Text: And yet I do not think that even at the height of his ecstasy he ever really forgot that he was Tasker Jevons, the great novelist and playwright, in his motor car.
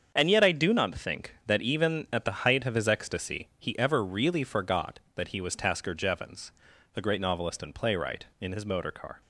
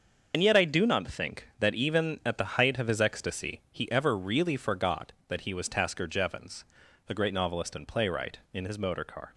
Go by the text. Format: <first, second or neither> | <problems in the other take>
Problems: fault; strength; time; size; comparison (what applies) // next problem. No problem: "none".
first | loses the start of "And"; at 0.3 s; 70 ms // starts louder than the rest; until 1.3 s; 6.5 dB; strong in the first